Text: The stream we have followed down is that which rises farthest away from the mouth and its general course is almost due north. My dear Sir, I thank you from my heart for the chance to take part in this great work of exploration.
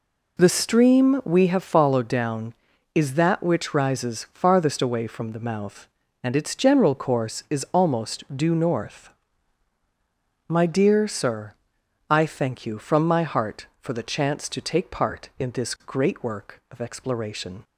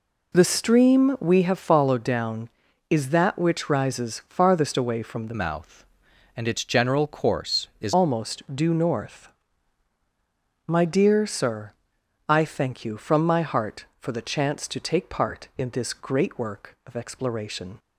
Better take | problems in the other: first | changes voice from "mouth" to "is"; from 5.3 to 7.9 s; 2.6 s long

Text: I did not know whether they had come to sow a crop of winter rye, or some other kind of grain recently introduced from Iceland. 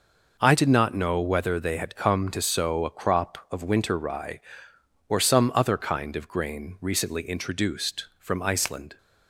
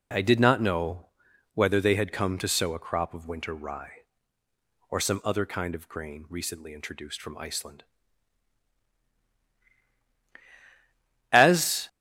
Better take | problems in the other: first | pauses between "know" and "whether"; noticeable; at 1.0 s; 0.48 s long // goes on to say "As"; from 11.3 s on; 0.56 s long

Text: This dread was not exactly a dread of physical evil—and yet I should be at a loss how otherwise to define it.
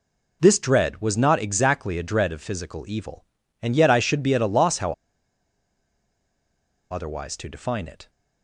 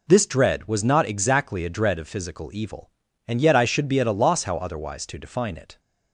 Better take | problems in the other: second | pauses between "how" and "otherwise"; strong; at 4.9 s; 1.9 s long

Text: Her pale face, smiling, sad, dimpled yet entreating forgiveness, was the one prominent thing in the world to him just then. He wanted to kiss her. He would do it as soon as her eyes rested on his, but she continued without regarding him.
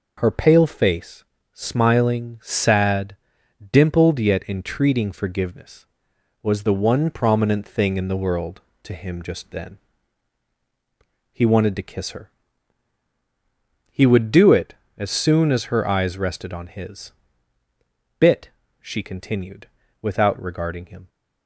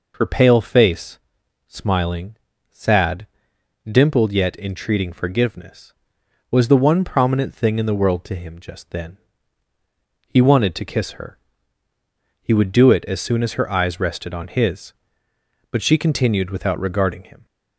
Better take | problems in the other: second | says "bit" for "but"; at 18.1 s // pauses between "continued" and "without"; slight; at 19.6 s; 0.34 s long

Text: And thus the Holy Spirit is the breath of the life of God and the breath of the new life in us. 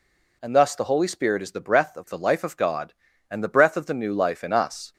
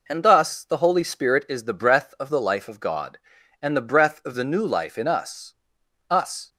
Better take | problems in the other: first | says "us" twice; at 6.0 s

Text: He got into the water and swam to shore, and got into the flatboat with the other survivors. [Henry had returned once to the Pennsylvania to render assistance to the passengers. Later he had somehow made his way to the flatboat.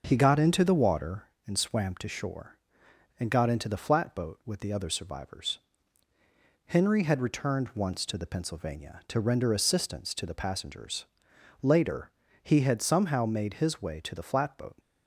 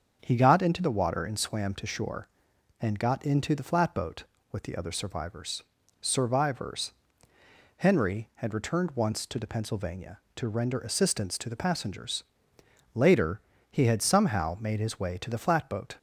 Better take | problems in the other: first | starts louder than the rest; until 1.2 s; 7 dB // says "survivors" twice; at 6.0 s // pauses between "Later" and "he"; slight; at 13.3 s; 0.32 s long; slight in the first

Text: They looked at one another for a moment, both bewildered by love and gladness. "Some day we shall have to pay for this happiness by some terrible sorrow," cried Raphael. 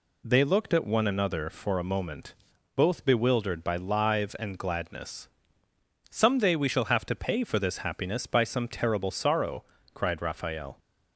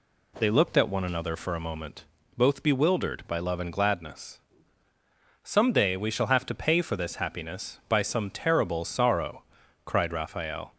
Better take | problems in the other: second | says "live" for "love"; at 3.7 s

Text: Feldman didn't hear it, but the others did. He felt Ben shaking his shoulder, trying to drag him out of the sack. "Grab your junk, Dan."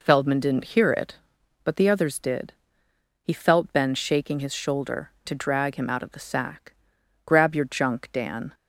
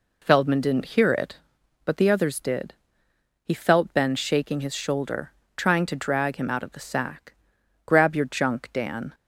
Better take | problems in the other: second | skips "trying"; at 5.1 s

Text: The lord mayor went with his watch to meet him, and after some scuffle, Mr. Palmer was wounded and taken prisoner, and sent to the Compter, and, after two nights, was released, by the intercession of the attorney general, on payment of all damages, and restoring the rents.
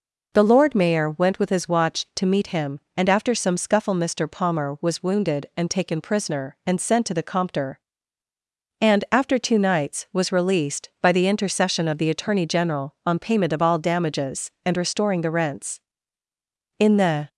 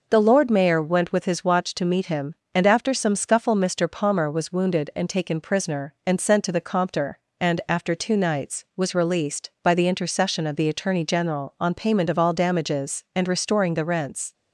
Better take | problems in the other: second | goes on to say "In the"; from 16.7 s on; 0.52 s long

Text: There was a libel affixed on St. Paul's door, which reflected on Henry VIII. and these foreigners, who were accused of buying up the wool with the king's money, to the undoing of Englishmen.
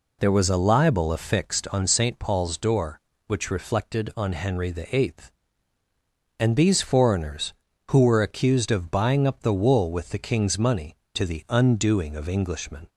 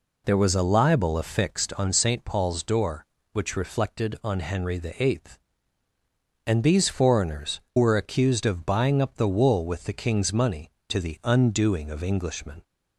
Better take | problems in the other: first | skips "who"; at 7.6 s

